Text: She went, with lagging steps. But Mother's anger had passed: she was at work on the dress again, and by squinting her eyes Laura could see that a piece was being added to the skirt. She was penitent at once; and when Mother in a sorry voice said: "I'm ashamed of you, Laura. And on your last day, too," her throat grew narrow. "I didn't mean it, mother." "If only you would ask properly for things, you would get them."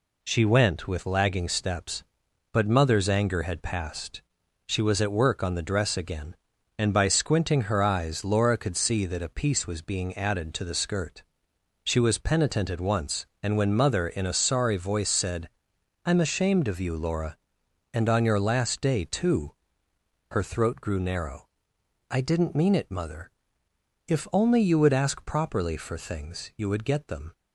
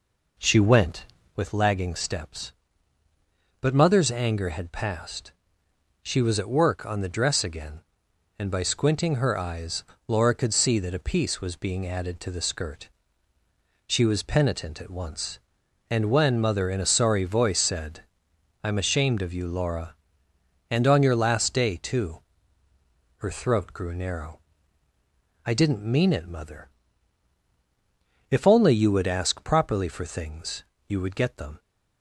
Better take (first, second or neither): first